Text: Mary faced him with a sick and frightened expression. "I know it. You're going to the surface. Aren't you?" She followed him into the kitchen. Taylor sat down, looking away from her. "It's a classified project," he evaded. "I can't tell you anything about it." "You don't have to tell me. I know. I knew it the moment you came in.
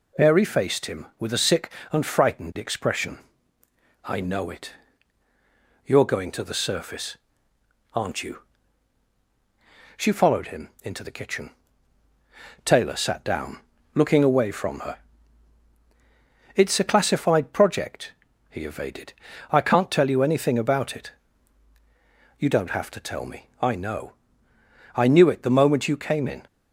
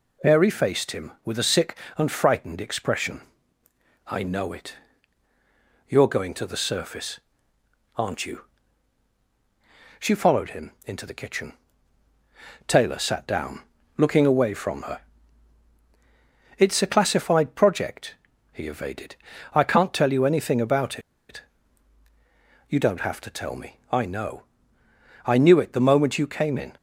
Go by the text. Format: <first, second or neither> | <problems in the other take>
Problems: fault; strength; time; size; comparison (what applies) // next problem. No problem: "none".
first | pauses between "about" and "it"; slight; at 20.9 s; 0.30 s long